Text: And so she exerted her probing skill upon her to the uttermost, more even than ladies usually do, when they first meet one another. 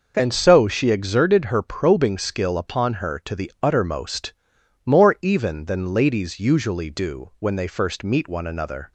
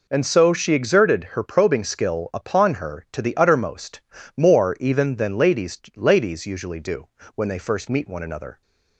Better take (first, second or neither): first